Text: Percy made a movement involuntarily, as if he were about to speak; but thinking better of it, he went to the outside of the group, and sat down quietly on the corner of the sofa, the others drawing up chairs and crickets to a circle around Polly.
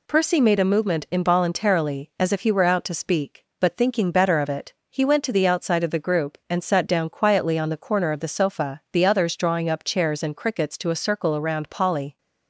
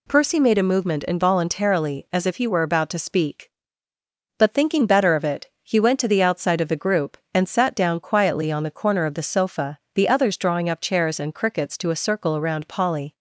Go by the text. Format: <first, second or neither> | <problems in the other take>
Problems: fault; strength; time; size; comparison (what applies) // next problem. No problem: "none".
second | says "out" for "about"; at 2.6 s